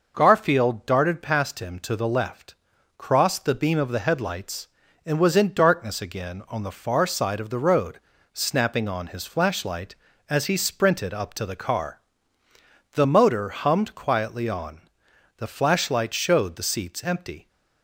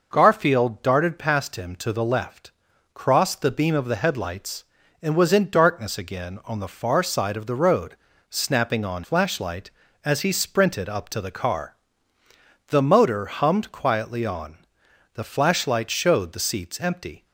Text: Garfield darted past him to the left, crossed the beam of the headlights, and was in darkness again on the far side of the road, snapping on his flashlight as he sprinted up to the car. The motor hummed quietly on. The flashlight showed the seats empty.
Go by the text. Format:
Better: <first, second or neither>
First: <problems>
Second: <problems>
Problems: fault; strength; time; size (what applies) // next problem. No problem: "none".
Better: first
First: none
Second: skips "his"; at 9.0 s